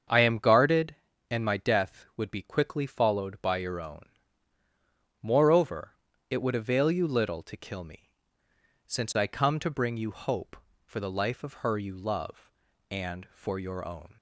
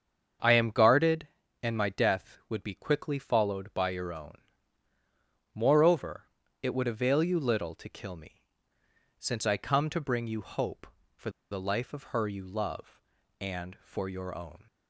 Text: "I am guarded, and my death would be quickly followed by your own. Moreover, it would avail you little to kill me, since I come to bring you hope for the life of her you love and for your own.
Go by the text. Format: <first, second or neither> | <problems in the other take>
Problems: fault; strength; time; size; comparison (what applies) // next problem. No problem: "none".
first | starts louder than the rest; strong; until 1.7 s; 7 dB; strong in the first // pauses between "for" and "the"; slight; at 11.2 s; 0.22 s long